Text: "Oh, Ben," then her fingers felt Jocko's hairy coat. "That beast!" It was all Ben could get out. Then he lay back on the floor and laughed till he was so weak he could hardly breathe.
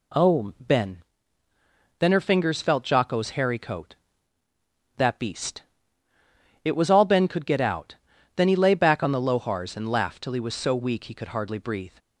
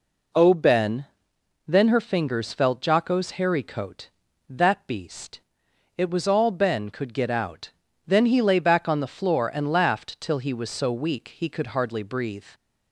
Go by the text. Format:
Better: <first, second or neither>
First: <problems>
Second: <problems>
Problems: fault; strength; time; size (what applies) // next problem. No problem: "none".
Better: second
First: says "lohars" for "floor"; at 9.2 s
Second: none